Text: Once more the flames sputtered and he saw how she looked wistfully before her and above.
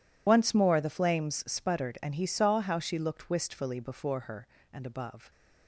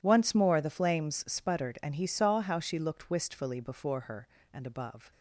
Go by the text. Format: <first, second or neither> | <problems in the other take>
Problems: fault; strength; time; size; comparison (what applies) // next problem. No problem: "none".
second | loses the start of "Once"; at 0.2 s; 45 ms